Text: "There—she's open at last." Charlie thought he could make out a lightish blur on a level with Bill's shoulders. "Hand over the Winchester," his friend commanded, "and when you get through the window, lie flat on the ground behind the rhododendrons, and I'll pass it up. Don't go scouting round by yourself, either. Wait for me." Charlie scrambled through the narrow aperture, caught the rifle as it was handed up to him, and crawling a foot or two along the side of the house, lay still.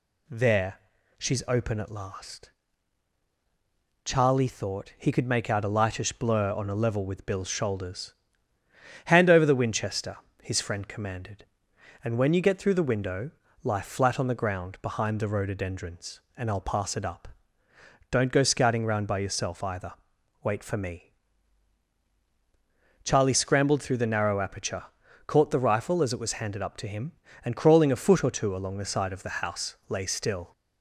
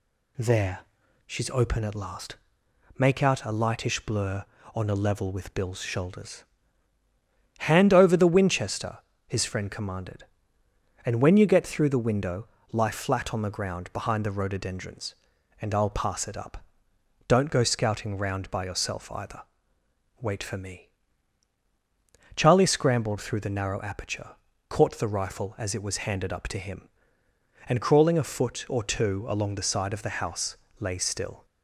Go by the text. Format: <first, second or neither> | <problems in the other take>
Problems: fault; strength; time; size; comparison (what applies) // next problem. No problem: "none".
first | skips "Charlie thought he could"; at 2.6 s